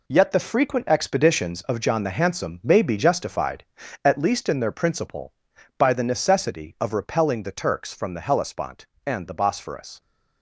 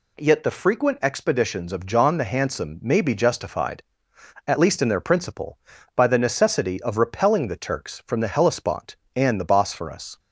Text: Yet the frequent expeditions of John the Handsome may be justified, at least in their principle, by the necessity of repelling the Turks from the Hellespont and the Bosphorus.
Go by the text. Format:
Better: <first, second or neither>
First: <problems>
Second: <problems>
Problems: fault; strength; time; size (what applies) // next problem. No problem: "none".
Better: second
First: gets quieter; strong; throughout; 8.5 dB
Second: none